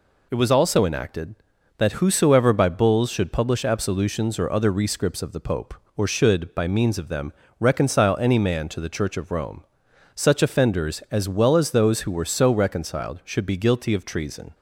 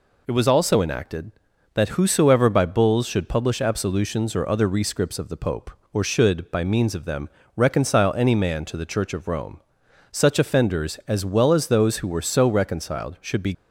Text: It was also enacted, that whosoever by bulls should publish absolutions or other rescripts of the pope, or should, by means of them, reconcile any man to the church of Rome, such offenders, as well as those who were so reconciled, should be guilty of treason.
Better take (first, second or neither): first